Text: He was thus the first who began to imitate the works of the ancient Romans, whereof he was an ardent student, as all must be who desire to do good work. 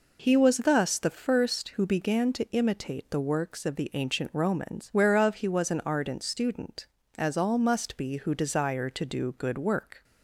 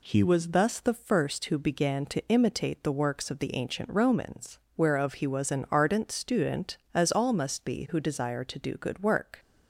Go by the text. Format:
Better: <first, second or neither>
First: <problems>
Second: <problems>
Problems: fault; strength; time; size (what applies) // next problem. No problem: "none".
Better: neither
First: none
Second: none